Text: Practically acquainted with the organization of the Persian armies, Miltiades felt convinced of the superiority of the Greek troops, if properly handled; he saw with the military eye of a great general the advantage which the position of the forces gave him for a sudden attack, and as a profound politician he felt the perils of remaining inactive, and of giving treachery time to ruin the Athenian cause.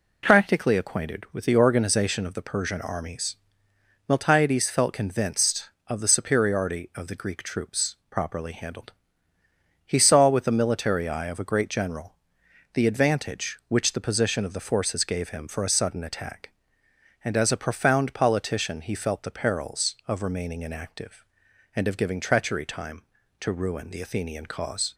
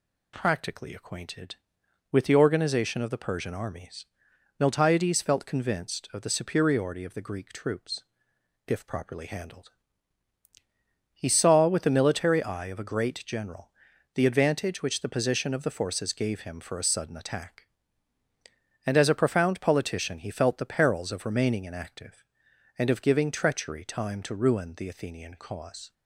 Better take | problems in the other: second | skips "if"; at 8.0 s // pauses between "general" and "the"; noticeable; at 12.1 s; 0.60 s long; also in the second

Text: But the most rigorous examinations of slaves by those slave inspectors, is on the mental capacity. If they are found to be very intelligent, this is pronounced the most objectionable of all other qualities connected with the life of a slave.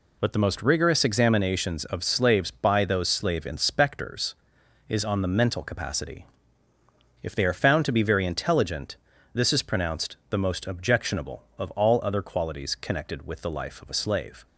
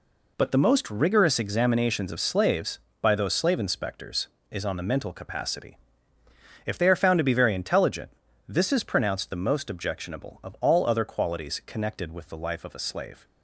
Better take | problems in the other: neither | none

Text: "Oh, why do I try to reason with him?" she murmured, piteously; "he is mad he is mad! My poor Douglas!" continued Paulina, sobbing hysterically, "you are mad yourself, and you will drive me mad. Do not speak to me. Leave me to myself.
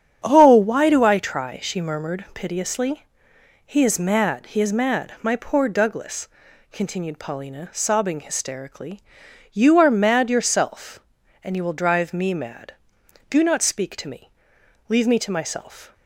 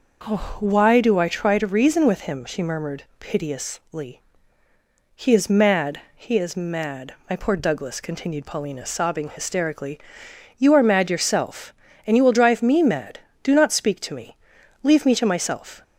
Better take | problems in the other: second | starts louder than the rest; strong; until 1.2 s; 8.5 dB // skips "to reason with him"; at 1.5 s

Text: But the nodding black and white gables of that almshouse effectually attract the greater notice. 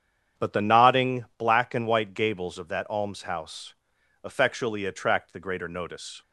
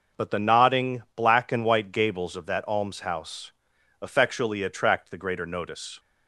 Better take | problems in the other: second | starts louder than the rest; strong; until 1.5 s; 8.5 dB // pauses between "almshouse" and "effectually"; noticeable; at 3.7 s; 0.50 s long; noticeable in the second

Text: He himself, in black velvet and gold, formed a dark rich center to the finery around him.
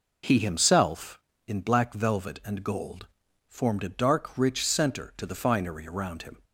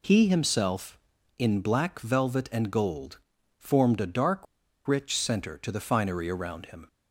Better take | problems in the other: first | pauses between "dark" and "rich"; at 4.4 s; 0.41 s long

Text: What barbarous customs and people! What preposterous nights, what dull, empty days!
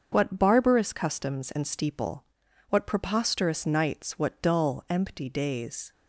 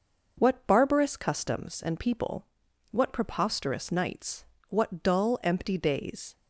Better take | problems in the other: second | starts louder than the rest; until 1.1 s; 6.5 dB // says "steeple" for "people"; at 1.6 s

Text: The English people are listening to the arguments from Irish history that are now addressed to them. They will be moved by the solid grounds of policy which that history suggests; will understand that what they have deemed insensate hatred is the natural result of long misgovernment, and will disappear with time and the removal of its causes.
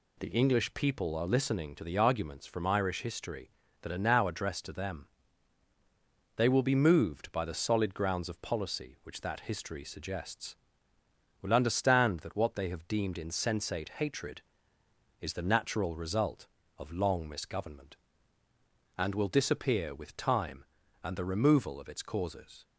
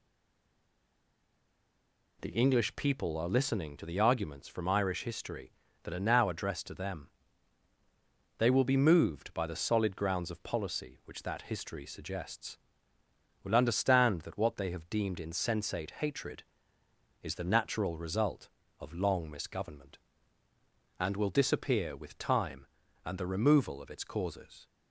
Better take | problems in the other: first | stays silent before the first word; until 2.1 s; 2.1 s long

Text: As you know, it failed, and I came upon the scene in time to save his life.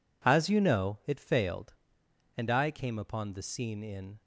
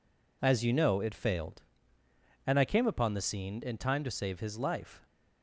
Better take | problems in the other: second | stops before "time to save his life"; at 4.2 s

